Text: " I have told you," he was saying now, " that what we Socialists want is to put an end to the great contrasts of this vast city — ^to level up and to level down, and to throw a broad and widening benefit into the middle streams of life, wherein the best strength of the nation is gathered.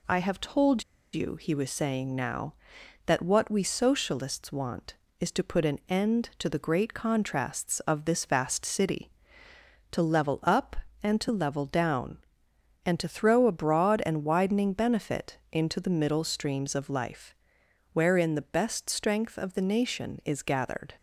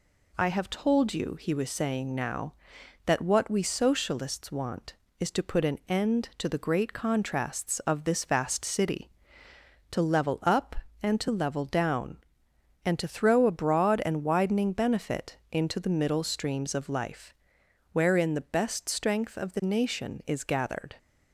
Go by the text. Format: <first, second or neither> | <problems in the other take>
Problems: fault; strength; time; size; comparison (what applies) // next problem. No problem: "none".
second | pauses between "told" and "you"; slight; at 0.8 s; 0.30 s long